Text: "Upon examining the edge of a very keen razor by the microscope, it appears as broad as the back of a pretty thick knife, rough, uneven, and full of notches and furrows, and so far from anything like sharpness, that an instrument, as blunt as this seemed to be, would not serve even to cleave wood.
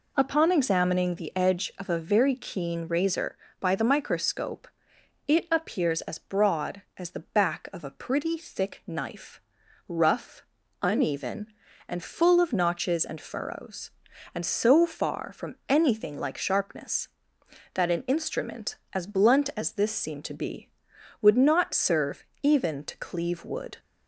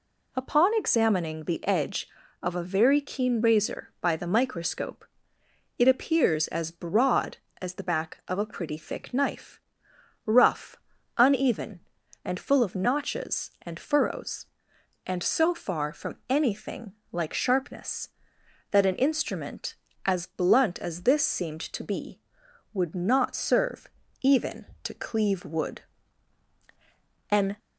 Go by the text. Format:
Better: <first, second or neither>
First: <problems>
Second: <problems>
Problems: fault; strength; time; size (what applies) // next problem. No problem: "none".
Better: first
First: pauses between "serve" and "even"; slight; at 22.2 s; 0.16 s long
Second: pauses between "anything" and "like"; slight; at 16.9 s; 0.18 s long // pauses between "serve" and "even"; slight; at 23.8 s; 0.34 s long // goes on to say "An"; slight; from 27.2 s on; 0.28 s long